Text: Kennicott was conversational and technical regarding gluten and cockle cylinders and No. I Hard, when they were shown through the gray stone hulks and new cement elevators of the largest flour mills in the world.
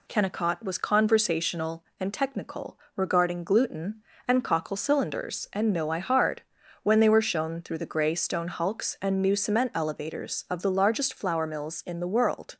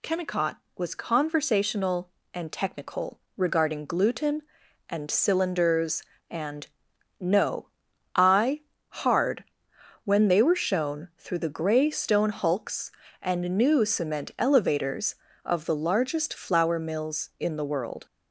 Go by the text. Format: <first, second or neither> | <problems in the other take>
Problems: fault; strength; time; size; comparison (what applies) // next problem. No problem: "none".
first | pauses between "technical" and "regarding"; slight; at 3.1 s; 0.18 s long; slight in the first // skips "cockle"; at 5.0 s // pauses between "and" and "No"; noticeable; at 6.6 s; 0.52 s long // pauses between "I" and "Hard"; slight; at 8.6 s; 0.28 s long